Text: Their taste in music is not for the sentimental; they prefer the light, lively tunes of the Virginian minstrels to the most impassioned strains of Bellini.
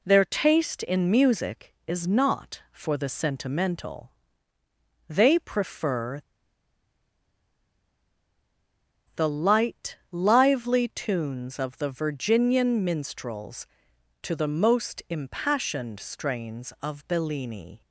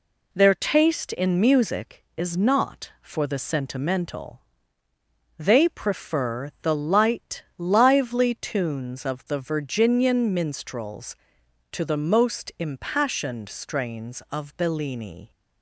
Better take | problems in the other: second | pauses between "prefer" and "the"; strong; at 6.2 s; 2.9 s long

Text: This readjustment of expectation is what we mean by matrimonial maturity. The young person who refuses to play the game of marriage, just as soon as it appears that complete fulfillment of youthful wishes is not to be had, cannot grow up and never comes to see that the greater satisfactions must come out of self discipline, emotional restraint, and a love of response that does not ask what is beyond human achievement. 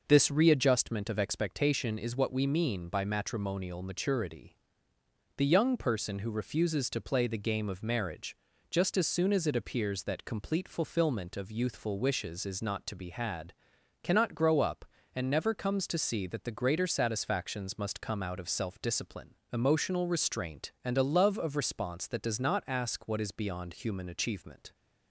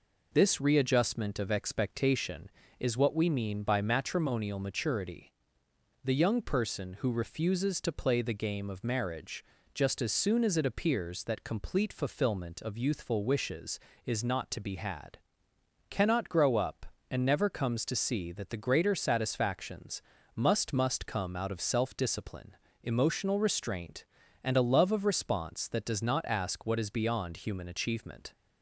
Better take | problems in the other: first | pauses between "satisfactions" and "must"; slight; at 20.0 s; 0.34 s long // says "must" twice; at 20.7 s

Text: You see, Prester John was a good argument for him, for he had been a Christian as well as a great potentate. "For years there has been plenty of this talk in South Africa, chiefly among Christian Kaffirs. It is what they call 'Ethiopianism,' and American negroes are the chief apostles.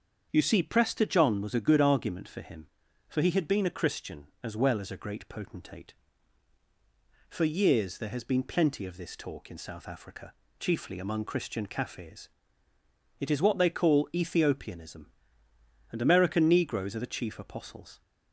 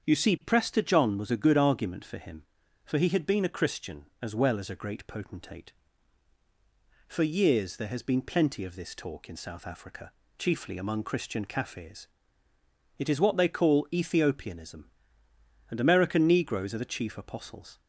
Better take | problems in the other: neither | starts louder than the rest; strong; the same in both

